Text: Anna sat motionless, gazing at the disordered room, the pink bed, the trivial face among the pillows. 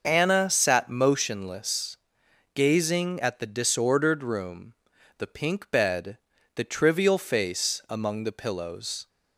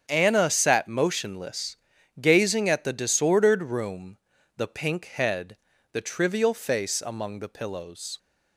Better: first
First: starts louder than the rest; noticeable; until 1.0 s; 6 dB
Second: starts louder than the rest; strong; until 1.1 s; 8 dB // says "head" for "bed"; at 5.0 s

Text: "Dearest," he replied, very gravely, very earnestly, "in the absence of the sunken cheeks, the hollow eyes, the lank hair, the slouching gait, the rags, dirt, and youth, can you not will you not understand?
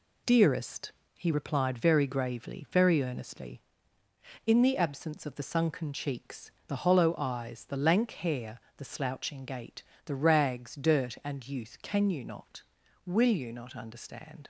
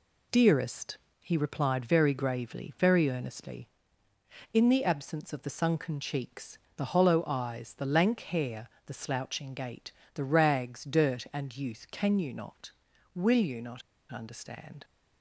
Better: first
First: none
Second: pauses between "not" and "understand"; slight; at 13.8 s; 0.30 s long

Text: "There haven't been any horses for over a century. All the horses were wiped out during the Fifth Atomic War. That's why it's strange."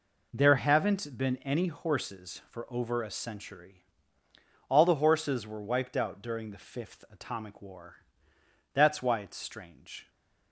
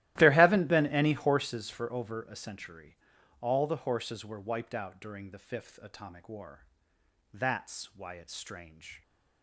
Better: first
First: none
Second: starts louder than the rest; strong; until 1.4 s; 15 dB

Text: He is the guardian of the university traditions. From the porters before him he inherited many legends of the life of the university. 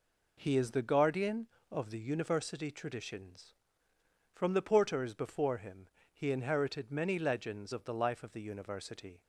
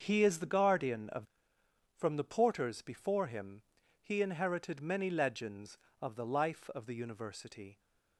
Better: first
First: pauses between "him" and "he"; slight; at 5.8 s; 0.24 s long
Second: starts louder than the rest; until 1.0 s; 6.5 dB // skips "the university traditions"; at 1.6 s // pauses between "him" and "he"; at 3.6 s; 0.40 s long

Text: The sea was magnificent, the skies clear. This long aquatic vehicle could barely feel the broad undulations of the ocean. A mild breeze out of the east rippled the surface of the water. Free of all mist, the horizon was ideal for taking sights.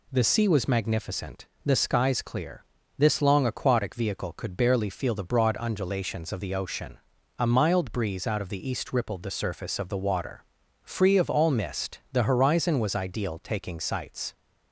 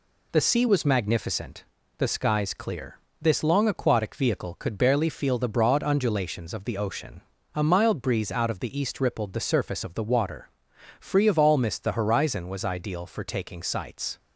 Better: second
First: skips "for"; at 13.4 s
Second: none

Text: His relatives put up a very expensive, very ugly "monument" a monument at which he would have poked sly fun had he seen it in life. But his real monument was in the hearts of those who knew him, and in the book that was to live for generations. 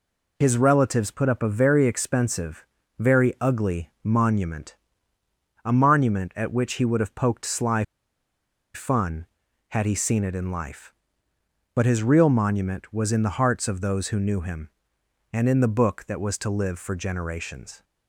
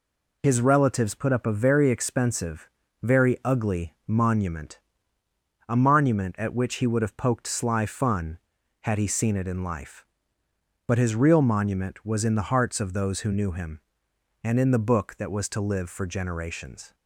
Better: second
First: pauses between "monument" and "a"; noticeable; at 4.7 s; 0.88 s long // pauses between "sly" and "fun"; noticeable; at 7.8 s; 0.92 s long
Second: pauses between "monument" and "a"; noticeable; at 4.7 s; 0.88 s long

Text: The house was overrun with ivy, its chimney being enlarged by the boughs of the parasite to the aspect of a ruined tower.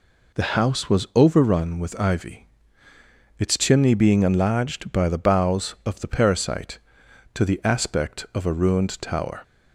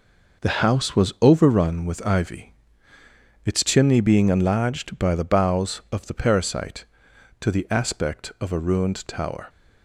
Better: first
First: none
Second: gets quieter; strong; throughout; 8 dB

